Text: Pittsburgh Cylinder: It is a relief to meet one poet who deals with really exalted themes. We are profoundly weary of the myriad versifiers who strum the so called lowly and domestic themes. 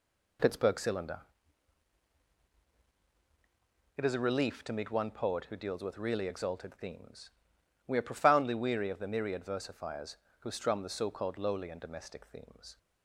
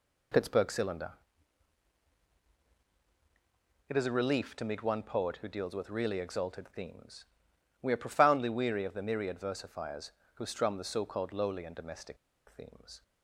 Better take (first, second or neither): first